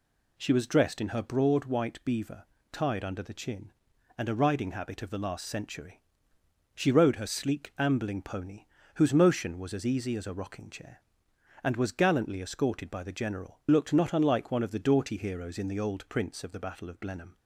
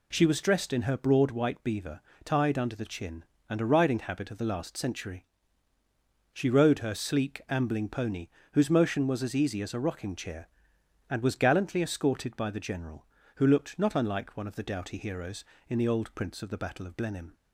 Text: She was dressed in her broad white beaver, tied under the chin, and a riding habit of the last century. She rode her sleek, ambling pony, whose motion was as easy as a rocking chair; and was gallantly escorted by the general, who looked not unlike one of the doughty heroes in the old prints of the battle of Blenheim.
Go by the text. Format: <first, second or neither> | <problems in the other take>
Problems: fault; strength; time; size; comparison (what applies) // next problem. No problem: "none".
second | skips "who"; at 13.6 s